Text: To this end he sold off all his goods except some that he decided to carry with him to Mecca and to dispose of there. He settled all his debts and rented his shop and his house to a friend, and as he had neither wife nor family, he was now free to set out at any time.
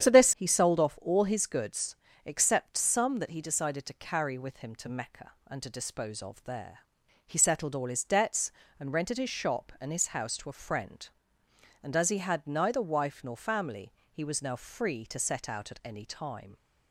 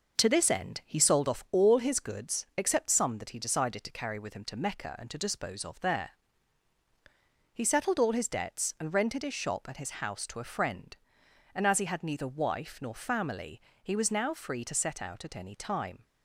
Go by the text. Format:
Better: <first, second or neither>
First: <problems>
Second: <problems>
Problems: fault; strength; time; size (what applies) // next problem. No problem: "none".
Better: second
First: starts louder than the rest; strong; until 1.0 s; 9 dB // skips "end"; at 0.3 s // pauses between "goods" and "except"; slight; at 1.9 s; 0.26 s long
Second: none